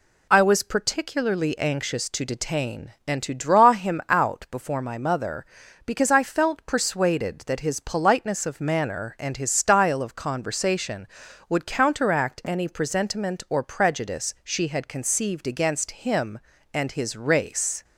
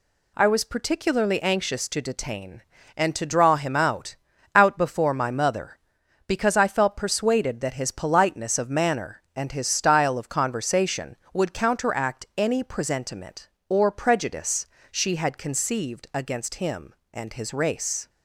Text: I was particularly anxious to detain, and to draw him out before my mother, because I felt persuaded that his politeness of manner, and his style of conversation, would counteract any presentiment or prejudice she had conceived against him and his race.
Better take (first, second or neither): first